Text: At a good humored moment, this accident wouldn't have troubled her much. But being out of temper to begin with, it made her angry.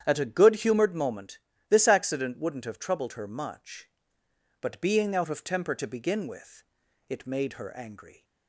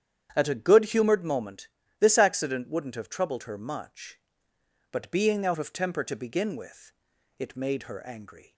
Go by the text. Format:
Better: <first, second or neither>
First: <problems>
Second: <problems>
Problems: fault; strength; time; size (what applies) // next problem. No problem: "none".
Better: neither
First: starts louder than the rest; strong; until 1.0 s; 9 dB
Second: starts louder than the rest; strong; until 1.3 s; 9 dB